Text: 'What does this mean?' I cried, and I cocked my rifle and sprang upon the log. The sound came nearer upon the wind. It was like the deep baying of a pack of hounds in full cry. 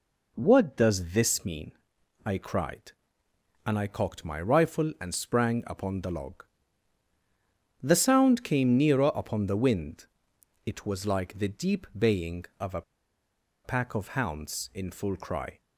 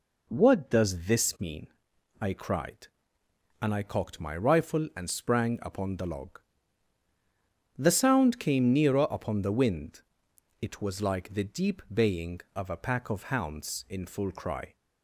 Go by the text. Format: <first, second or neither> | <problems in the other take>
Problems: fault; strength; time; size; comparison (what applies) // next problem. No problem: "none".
second | pauses between "a" and "pack"; noticeable; at 12.8 s; 0.82 s long